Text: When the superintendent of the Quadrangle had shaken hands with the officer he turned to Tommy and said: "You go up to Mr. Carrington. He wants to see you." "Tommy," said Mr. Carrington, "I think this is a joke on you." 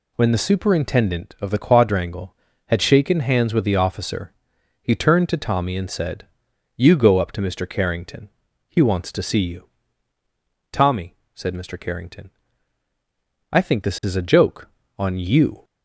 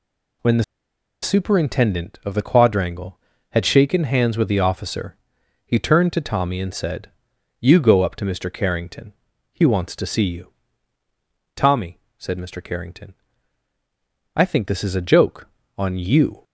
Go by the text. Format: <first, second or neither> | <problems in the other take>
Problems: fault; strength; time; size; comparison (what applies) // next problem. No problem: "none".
first | pauses between "the" and "superintendent"; noticeable; at 0.6 s; 0.59 s long // pauses between "officer" and "he"; noticeable; at 5.1 s; 0.48 s long; noticeable in the first